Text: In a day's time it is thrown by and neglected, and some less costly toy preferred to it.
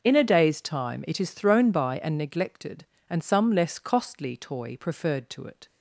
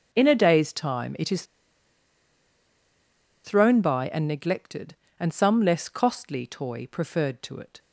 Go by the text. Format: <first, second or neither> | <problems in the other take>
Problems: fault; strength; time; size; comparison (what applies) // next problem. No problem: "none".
first | pauses between "is" and "thrown"; strong; at 1.4 s; 2.0 s long